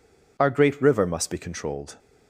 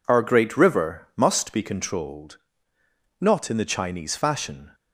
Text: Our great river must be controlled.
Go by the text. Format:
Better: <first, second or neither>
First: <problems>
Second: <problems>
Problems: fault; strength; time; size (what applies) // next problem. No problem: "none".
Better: first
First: none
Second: goes on to say "Not in the Chinese fashion"; from 3.2 s on; 1.5 s long